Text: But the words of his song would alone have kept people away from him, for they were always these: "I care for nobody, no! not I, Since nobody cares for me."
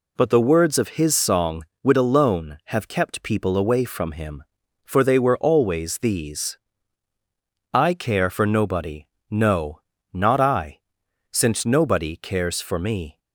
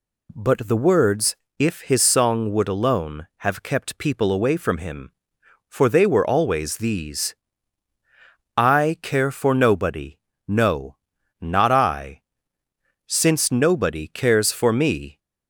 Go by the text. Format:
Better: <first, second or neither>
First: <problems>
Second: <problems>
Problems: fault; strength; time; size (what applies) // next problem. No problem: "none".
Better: first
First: none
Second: says "if" for "of"; at 1.5 s